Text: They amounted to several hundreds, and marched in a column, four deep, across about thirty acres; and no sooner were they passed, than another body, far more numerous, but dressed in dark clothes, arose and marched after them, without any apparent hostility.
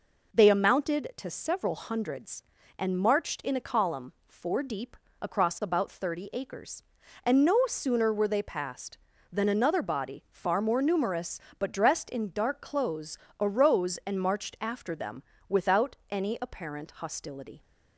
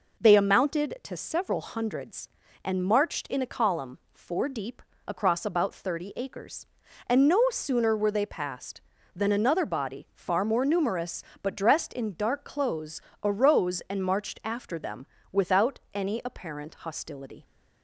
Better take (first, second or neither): neither